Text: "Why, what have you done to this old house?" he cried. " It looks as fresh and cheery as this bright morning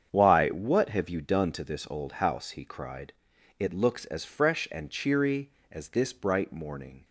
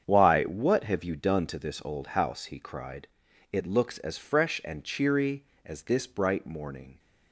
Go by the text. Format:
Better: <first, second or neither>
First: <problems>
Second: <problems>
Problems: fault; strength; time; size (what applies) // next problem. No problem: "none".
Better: neither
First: starts louder than the rest; strong; until 1.1 s; 8 dB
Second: starts louder than the rest; strong; until 1.0 s; 8 dB